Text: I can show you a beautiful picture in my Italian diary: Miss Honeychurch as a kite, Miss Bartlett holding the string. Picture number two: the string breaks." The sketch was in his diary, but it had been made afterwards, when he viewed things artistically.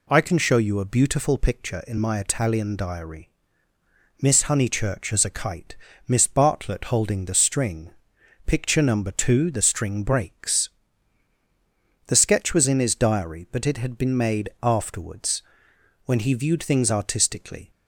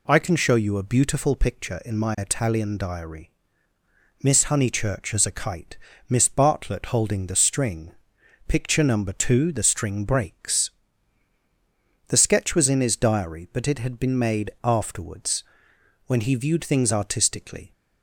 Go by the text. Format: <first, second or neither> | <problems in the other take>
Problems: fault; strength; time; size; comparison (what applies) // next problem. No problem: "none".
neither | none